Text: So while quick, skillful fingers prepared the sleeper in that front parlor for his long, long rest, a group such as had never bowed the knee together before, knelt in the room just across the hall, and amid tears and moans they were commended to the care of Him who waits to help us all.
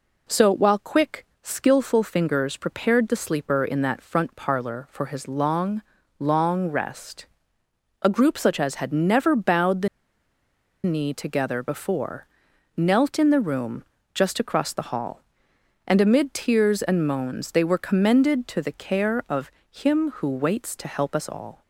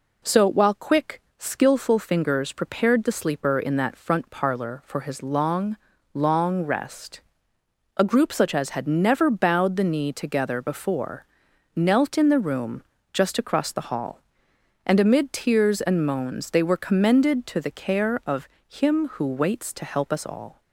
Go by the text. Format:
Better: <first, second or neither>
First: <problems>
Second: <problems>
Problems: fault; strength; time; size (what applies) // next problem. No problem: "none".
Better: second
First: pauses between "the" and "knee"; noticeable; at 9.8 s; 0.96 s long // pauses between "room" and "just"; slight; at 13.8 s; 0.30 s long // pauses between "of" and "Him"; slight; at 19.5 s; 0.20 s long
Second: pauses between "room" and "just"; slight; at 12.8 s; 0.30 s long // pauses between "of" and "Him"; slight; at 18.4 s; 0.20 s long